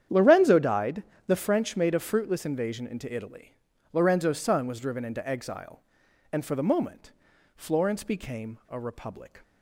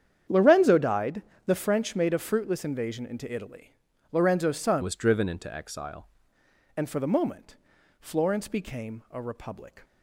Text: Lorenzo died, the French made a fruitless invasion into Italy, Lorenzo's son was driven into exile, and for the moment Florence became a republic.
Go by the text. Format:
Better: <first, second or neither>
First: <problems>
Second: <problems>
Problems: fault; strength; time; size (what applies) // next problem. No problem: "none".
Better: first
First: starts louder than the rest; strong; until 1.3 s; 9.5 dB // pauses between "moment" and "Florence"; at 7.1 s; 0.44 s long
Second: starts louder than the rest; strong; until 1.5 s; 9 dB // changes voice from "was" to "exile"; from 4.8 to 6.0 s; 1.2 s long // pauses between "moment" and "Florence"; at 7.5 s; 0.44 s long